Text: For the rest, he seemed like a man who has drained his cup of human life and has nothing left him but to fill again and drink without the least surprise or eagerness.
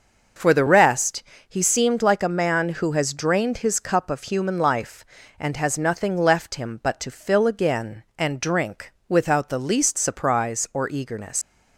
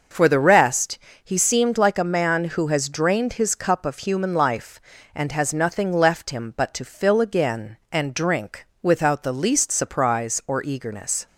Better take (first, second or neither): second